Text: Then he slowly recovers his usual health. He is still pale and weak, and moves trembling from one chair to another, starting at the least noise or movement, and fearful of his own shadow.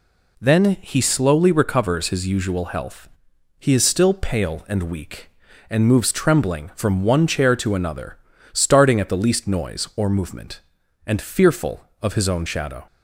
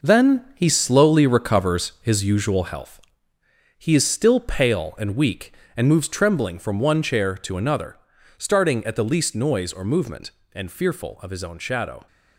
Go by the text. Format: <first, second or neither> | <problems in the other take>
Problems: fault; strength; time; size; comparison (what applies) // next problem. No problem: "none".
first | gets quieter; strong; throughout; 8.5 dB